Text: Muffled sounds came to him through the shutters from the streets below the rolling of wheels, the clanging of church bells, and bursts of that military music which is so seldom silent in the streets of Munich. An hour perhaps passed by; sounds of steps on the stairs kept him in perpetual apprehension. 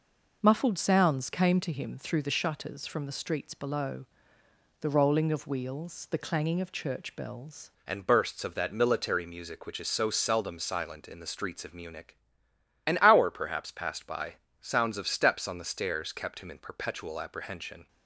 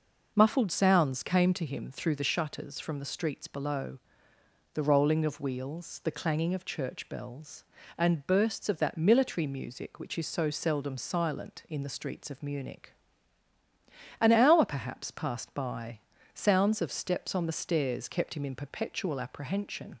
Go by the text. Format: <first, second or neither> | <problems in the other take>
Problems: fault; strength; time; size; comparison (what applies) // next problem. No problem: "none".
second | pauses between "below" and "the"; noticeable; at 4.0 s; 0.74 s long; noticeable in the second // changes voice at "and"; from 7.8 s on; 10.0 s long